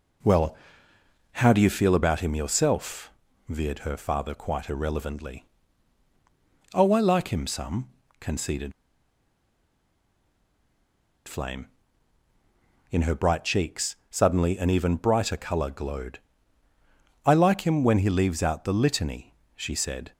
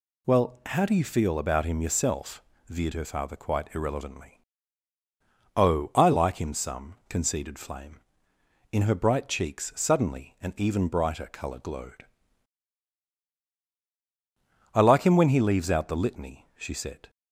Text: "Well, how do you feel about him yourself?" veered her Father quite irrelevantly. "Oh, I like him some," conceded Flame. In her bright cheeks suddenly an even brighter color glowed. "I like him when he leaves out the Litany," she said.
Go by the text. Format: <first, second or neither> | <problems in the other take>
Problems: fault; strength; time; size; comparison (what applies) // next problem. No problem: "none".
second | pauses between "conceded" and "Flame"; strong; at 8.7 s; 2.5 s long